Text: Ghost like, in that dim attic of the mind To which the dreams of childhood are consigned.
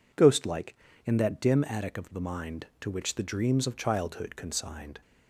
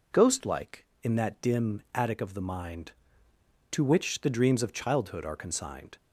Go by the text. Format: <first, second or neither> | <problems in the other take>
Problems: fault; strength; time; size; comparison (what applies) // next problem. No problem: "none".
second | skips "are"; at 4.3 s